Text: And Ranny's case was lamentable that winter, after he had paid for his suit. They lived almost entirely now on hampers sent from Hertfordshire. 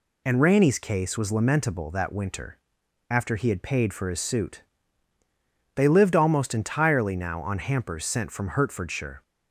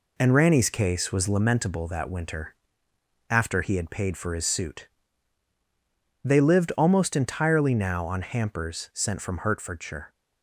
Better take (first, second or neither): first